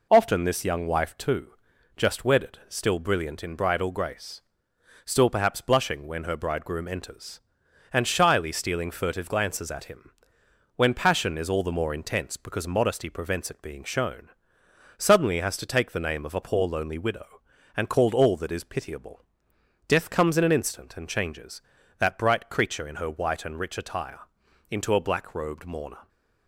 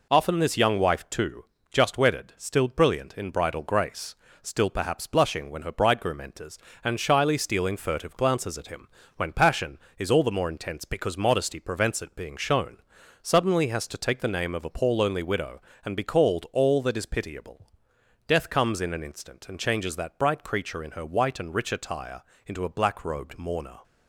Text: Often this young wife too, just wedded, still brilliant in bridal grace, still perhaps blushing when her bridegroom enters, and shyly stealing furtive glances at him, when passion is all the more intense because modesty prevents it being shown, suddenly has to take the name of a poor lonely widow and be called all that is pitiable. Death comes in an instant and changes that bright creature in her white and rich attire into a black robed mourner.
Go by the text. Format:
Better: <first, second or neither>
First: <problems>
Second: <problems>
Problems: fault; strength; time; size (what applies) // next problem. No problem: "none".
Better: second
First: skips "be"; at 17.9 s // pauses between "attire" and "into"; noticeable; at 24.2 s; 0.50 s long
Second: pauses between "attire" and "into"; slight; at 22.2 s; 0.24 s long